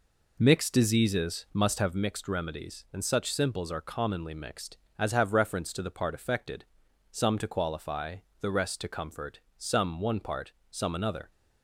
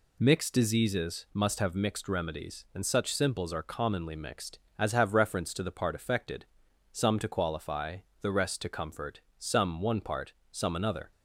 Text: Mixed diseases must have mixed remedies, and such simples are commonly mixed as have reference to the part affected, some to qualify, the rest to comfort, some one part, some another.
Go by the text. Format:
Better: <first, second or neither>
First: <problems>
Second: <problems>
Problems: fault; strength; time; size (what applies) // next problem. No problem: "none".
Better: second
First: starts louder than the rest; noticeable; until 2.0 s; 4 dB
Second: none